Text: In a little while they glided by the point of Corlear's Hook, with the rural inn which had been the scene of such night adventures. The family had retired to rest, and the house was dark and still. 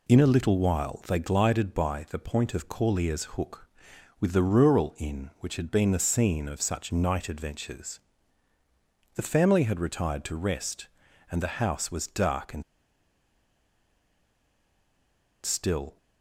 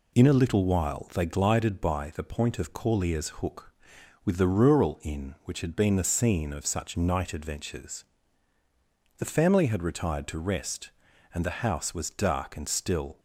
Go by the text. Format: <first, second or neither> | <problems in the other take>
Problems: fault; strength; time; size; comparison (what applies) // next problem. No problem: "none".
second | pauses between "and" and "still"; strong; at 12.6 s; 2.8 s long